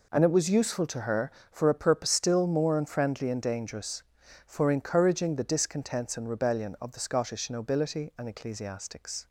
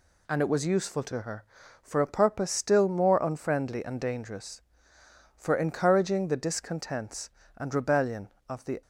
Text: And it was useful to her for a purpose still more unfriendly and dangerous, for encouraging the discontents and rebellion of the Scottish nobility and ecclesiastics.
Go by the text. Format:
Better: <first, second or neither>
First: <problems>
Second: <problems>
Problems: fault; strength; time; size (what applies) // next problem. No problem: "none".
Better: first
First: none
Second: stops before "Scottish nobility and ecclesiastics"; at 8.8 s